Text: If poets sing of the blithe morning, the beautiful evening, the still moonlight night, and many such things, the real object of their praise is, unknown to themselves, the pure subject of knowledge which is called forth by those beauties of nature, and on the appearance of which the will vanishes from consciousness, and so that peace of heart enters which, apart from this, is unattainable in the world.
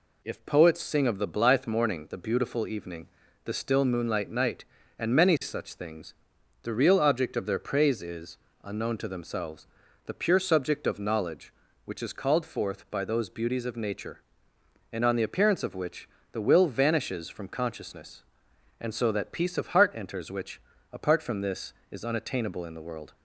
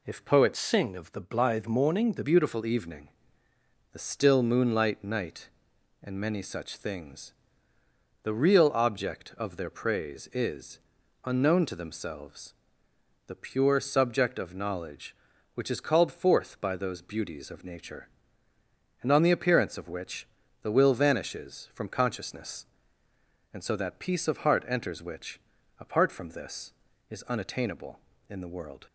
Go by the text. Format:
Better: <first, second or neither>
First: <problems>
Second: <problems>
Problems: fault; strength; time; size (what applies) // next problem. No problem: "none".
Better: first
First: pauses between "which" and "the"; slight; at 16.0 s; 0.24 s long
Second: changes voice from "sing" to "the"; from 0.5 to 2.2 s; 1.7 s long // pauses between "which" and "the"; slight; at 20.2 s; 0.34 s long